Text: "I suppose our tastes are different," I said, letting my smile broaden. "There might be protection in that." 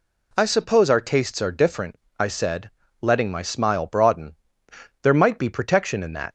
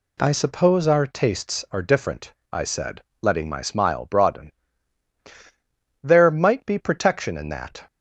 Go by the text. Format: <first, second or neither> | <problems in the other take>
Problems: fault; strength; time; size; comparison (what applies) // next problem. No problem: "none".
neither | none